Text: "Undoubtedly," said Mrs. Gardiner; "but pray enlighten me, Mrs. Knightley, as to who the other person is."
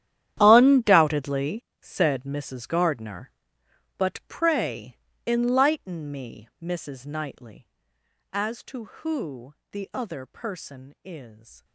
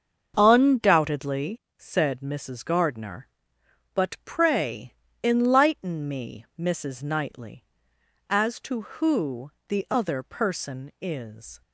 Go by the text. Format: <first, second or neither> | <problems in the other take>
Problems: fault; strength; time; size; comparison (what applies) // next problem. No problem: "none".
second | gets quieter; strong; throughout; 17 dB // starts louder than the rest; strong; until 1.4 s; 11 dB; also in the second // pauses between "pray" and "enlighten"; slight; at 4.9 s; 0.30 s long; slight in the second // pauses between "who" and "the"; slight; at 9.5 s; 0.18 s long; slight in the second